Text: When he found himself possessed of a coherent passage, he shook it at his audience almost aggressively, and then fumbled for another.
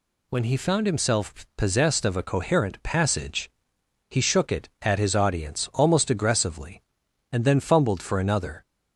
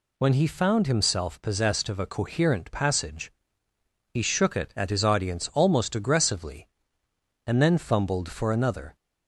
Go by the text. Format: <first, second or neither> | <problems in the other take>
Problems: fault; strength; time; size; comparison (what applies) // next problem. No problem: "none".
neither | none